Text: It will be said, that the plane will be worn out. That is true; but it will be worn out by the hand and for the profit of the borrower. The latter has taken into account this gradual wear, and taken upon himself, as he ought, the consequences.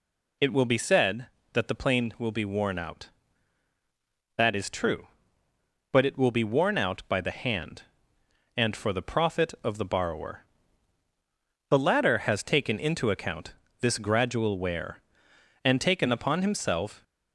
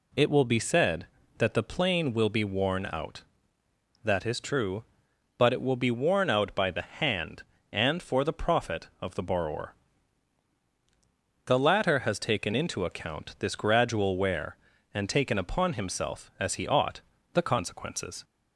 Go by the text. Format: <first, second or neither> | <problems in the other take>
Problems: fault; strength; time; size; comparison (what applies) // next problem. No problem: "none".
second | pauses between "account" and "this"; slight; at 13.5 s; 0.28 s long // stops before "as he ought the consequences"; at 17.0 s